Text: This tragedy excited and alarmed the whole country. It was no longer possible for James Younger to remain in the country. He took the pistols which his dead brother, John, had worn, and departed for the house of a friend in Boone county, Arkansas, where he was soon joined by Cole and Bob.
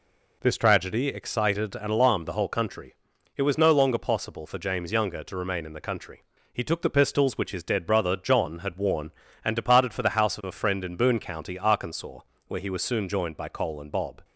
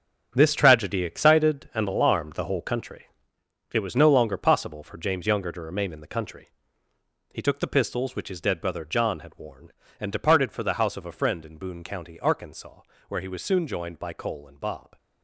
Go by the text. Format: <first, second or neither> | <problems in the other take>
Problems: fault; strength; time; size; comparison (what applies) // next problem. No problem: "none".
first | gets quieter; strong; throughout; 11 dB